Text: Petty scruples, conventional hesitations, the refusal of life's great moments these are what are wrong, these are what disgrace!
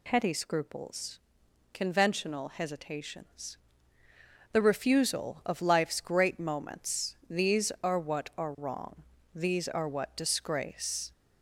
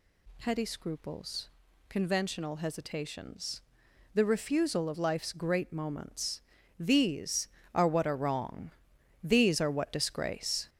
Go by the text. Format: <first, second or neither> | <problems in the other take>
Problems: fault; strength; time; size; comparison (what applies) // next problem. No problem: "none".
first | gets louder; noticeable; throughout; 6 dB // pauses between "moments" and "these"; slight; at 6.4 s; 0.36 s long